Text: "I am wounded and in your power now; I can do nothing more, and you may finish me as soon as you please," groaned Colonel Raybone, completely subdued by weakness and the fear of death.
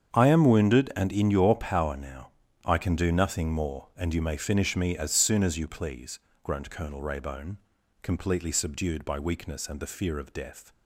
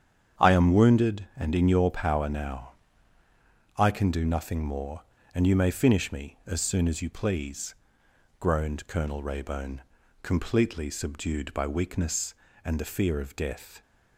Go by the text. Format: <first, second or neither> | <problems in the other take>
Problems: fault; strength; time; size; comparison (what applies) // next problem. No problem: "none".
neither | starts louder than the rest; strong; the same in both